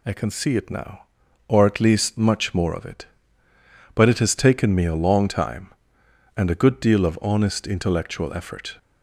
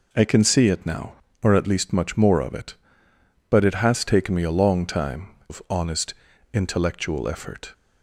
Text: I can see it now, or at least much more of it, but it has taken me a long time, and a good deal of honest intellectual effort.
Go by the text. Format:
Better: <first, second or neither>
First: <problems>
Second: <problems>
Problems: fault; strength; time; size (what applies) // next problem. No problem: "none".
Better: first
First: none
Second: skips "and a good deal"; at 5.3 s // pauses between "honest" and "intellectual"; at 6.1 s; 0.40 s long